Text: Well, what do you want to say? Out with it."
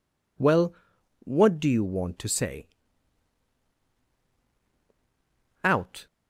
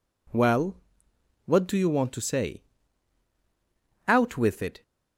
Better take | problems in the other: second | stops before "with it"; at 6.0 s

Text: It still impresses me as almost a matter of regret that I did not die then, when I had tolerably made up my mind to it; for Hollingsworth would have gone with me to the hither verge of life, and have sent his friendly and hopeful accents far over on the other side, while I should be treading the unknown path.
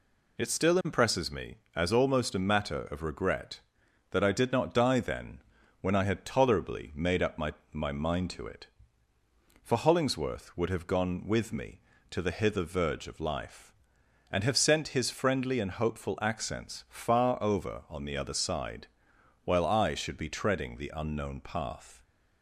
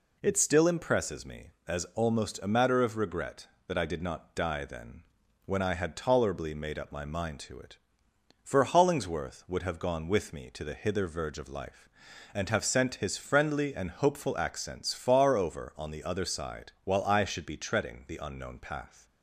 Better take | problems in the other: second | says "my" twice; at 7.7 s

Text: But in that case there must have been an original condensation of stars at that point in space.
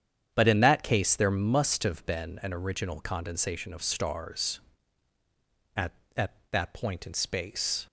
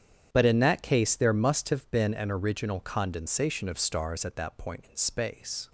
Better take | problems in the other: second | starts louder than the rest; strong; until 1.3 s; 8.5 dB; strong in the second // says "at" twice; at 6.1 s

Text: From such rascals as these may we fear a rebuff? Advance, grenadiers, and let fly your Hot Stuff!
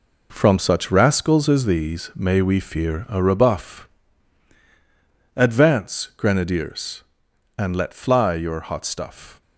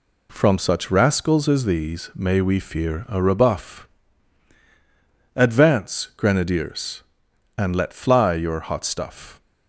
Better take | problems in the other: second | gets quieter; strong; throughout; 8.5 dB

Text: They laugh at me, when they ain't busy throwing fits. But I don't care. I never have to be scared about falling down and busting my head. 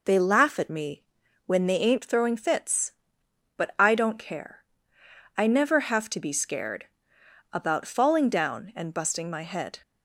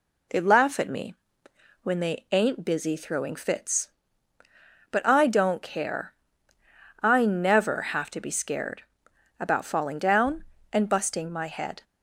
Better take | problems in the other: second | skips "busy"; at 2.0 s // pauses between "scared" and "about"; noticeable; at 6.8 s; 0.66 s long; noticeable in the second

